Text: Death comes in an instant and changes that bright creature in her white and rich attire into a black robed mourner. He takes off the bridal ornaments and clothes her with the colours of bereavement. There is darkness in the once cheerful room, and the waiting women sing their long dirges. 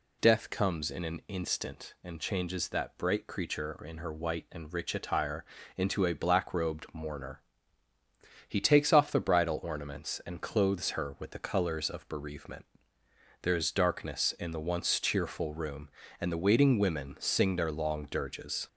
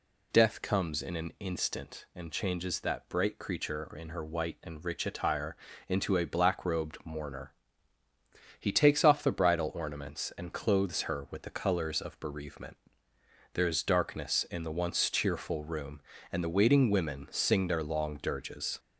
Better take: neither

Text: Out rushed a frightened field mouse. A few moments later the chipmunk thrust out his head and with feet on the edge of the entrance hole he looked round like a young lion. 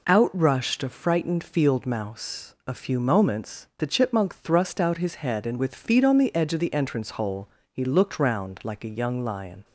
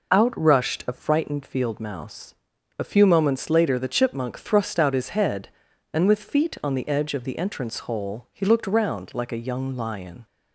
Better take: second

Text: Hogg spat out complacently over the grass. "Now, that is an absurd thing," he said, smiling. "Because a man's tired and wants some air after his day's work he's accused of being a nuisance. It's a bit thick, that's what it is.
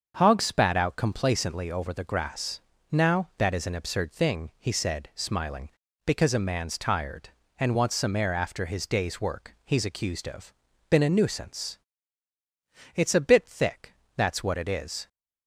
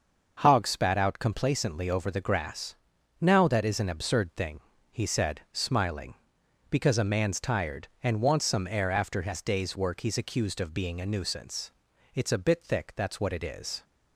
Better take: second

